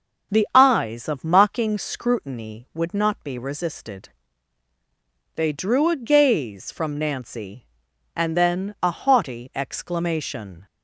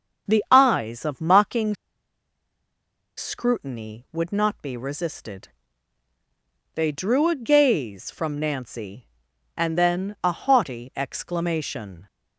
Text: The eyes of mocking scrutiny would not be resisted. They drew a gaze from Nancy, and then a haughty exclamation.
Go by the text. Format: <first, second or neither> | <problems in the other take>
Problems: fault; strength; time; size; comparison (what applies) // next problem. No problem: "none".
first | starts louder than the rest; until 1.3 s; 7 dB; also in the first // pauses between "mocking" and "scrutiny"; strong; at 1.7 s; 1.4 s long